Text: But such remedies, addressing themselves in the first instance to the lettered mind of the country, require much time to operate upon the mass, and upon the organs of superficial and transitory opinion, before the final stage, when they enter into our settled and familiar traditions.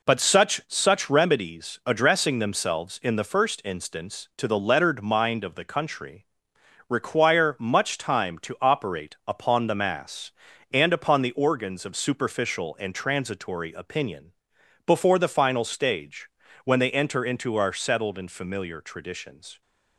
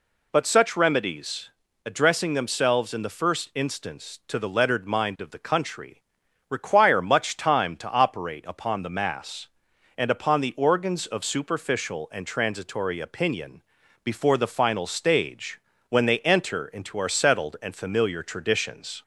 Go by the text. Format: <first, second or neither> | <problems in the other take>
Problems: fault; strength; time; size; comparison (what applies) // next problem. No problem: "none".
second | says "such" twice; at 0.6 s